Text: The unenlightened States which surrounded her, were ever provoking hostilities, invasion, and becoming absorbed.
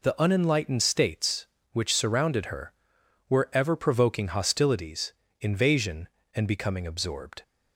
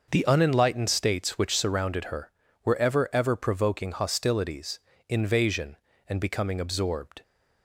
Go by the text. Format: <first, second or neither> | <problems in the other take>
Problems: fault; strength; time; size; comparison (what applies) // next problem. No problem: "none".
first | says "ever" twice; at 3.1 s